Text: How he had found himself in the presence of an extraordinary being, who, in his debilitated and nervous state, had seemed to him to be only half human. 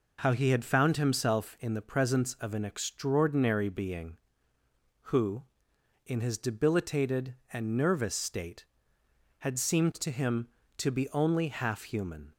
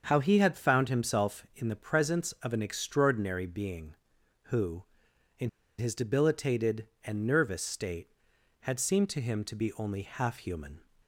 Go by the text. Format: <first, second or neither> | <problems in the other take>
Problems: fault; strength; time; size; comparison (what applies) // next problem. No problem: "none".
first | starts louder than the rest; until 1.0 s; 6.5 dB // pauses between "in" and "his"; slight; at 5.4 s; 0.30 s long